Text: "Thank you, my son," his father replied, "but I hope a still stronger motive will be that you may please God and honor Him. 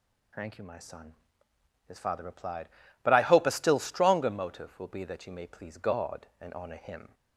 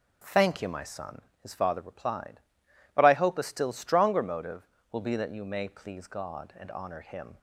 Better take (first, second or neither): neither